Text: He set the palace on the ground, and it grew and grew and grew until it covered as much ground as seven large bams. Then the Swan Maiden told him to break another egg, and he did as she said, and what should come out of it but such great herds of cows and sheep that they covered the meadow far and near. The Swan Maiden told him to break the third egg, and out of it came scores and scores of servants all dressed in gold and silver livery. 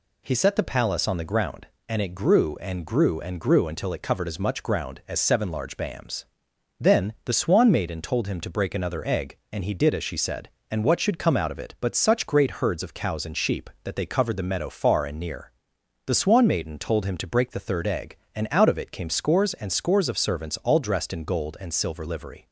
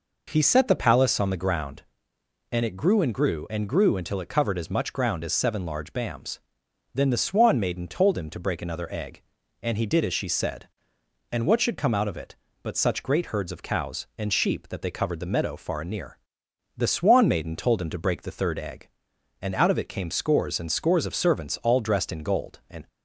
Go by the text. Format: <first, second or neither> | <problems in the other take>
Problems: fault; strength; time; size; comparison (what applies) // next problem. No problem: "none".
first | stops before "silver livery"; at 22.8 s